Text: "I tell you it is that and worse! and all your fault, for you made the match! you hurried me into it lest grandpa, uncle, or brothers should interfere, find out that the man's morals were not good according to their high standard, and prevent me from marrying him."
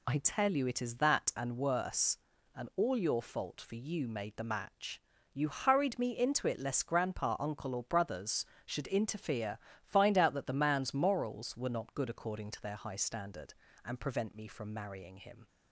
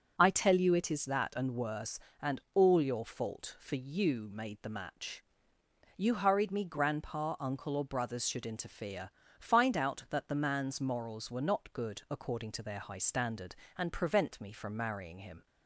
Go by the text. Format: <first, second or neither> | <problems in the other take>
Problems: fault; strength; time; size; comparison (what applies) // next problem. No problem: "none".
first | skips "into it lest"; at 6.6 s